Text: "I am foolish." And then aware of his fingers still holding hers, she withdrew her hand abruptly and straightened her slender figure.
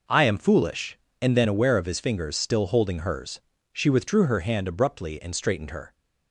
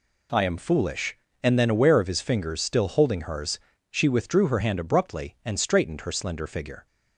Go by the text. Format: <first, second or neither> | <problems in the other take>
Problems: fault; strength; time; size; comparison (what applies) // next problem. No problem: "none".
second | stops before "slender figure"; at 5.9 s